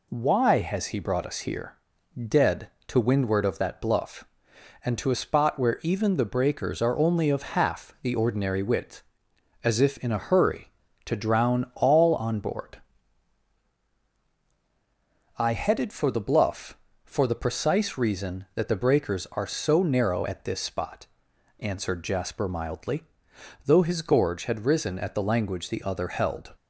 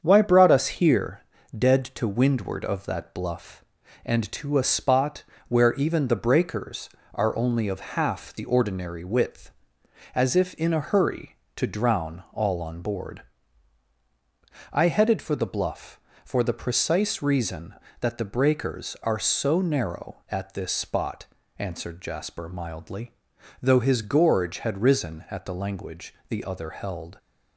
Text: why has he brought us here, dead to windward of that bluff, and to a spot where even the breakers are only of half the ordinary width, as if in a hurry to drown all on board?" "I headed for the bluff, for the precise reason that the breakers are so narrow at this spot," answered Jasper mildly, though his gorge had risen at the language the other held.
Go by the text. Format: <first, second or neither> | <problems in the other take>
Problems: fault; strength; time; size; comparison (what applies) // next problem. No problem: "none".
first | starts louder than the rest; strong; until 1.0 s; 7.5 dB // skips "has he"; at 0.2 s // pauses between "spot" and "where"; slight; at 5.2 s; 0.26 s long // pauses between "language" and "the"; slight; at 26.1 s; 0.16 s long